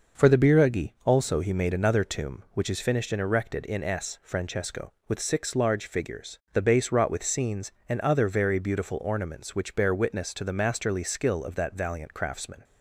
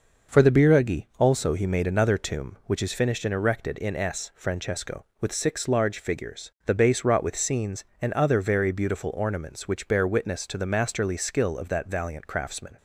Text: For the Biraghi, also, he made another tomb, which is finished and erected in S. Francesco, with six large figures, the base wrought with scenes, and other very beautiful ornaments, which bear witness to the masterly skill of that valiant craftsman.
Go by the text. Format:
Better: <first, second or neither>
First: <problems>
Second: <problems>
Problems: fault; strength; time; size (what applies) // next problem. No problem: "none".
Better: neither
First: none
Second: none